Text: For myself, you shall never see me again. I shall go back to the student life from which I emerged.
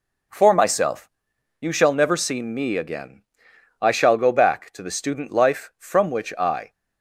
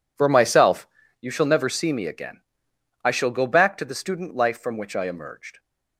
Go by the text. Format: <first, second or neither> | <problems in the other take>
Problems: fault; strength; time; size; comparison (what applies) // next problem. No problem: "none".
second | stops before "emerged"; at 6.7 s